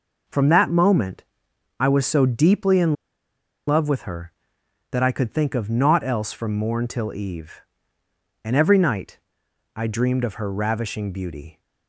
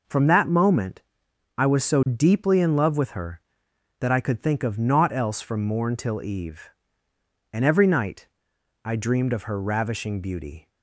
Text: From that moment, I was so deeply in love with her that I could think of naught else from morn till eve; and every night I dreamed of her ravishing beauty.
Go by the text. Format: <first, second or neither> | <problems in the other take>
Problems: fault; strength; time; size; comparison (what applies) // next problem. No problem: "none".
second | pauses between "in" and "love"; noticeable; at 2.9 s; 0.73 s long // pauses between "night" and "I"; noticeable; at 9.1 s; 0.56 s long; noticeable in the second